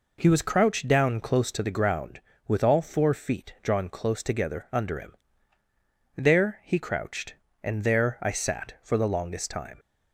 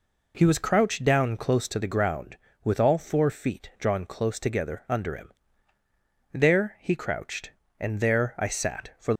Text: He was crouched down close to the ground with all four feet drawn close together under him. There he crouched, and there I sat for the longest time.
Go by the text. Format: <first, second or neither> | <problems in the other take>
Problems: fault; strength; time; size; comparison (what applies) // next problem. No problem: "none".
first | stops before "the longest time"; at 9.1 s